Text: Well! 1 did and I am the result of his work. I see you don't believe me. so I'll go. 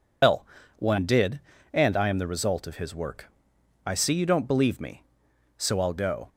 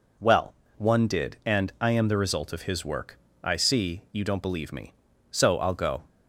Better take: second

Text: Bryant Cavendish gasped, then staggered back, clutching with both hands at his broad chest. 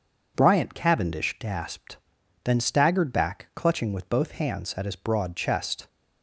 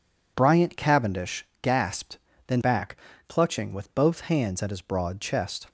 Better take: first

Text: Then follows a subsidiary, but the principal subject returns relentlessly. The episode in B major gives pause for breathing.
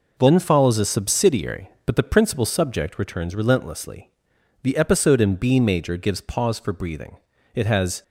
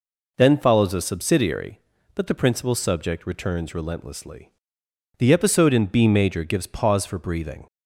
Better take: second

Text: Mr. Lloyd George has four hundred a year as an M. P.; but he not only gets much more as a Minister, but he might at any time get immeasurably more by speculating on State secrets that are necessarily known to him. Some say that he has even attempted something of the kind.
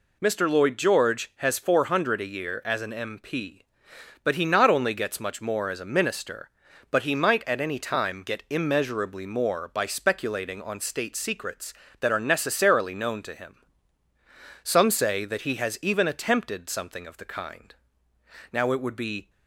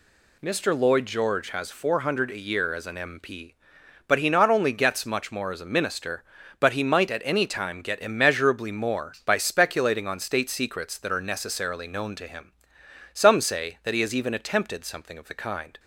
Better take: second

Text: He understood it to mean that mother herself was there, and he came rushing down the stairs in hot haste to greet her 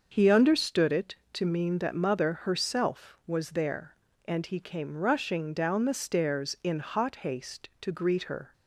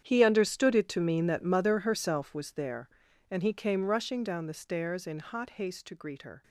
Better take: first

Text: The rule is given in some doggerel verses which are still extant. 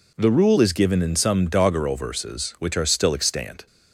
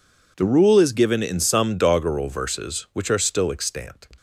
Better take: neither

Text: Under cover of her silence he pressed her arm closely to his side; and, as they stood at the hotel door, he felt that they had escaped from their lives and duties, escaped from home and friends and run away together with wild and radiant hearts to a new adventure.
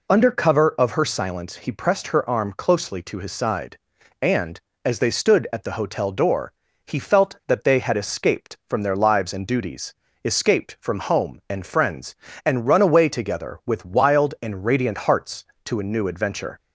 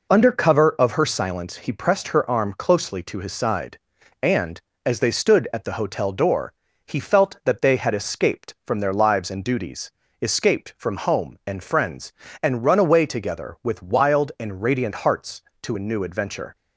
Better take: first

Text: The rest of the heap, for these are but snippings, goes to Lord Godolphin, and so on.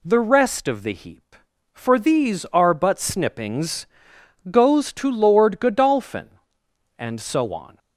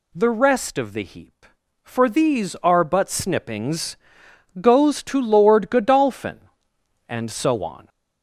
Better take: first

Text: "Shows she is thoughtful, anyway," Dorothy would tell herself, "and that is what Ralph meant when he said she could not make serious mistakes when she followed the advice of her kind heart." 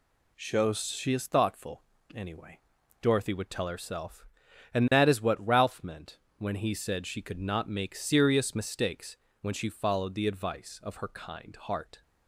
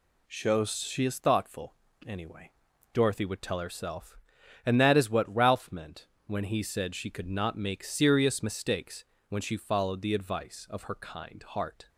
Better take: neither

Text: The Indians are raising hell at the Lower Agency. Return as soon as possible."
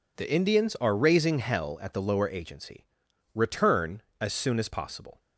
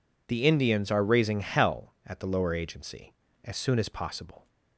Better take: first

